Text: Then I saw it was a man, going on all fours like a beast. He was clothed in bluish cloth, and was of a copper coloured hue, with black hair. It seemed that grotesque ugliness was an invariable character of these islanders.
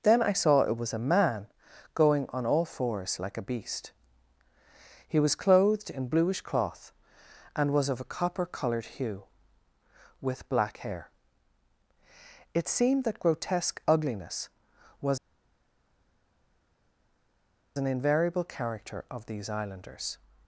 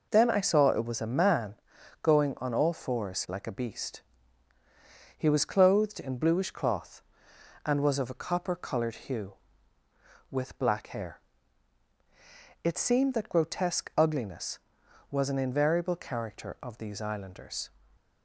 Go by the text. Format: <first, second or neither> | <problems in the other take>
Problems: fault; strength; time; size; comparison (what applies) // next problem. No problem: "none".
second | pauses between "was" and "an"; strong; at 15.1 s; 2.5 s long